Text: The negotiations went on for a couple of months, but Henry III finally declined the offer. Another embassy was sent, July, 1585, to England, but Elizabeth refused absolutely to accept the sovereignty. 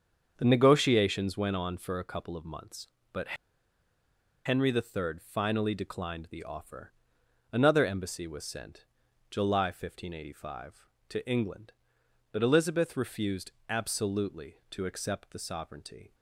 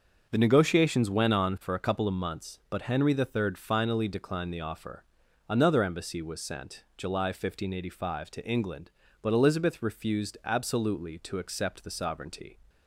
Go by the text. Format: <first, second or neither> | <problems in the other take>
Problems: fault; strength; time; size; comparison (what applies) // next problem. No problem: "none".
second | starts louder than the rest; until 1.3 s; 7 dB; also in the second // pauses between "but" and "Henry"; at 3.3 s; 1.1 s long // pauses between "refused" and "absolutely"; slight; at 13.5 s; 0.18 s long